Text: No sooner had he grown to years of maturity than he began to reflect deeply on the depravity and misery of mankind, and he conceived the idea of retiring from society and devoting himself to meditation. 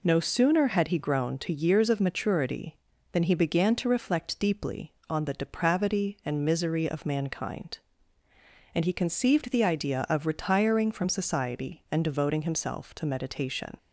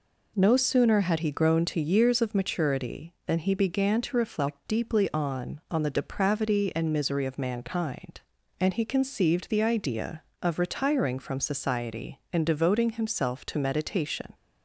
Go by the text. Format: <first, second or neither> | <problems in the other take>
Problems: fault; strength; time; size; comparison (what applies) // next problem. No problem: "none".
first | says "on" twice; at 5.6 s